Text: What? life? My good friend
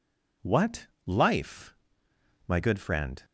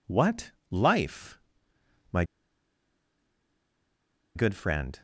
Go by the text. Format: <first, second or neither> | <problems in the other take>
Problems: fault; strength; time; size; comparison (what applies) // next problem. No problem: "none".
first | pauses between "My" and "good"; strong; at 2.2 s; 2.1 s long